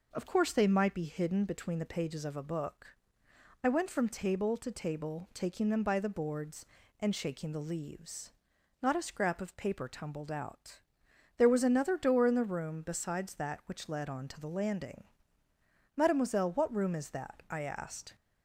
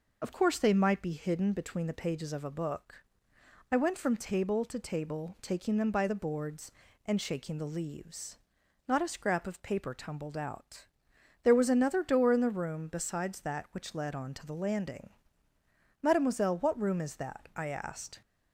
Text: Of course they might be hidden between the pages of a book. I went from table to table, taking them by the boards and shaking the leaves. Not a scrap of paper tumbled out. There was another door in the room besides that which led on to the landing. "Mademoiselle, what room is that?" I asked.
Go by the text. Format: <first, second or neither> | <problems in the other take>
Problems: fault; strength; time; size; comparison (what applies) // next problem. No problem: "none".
first | loses the start of "Of"; at 0.2 s; 30 ms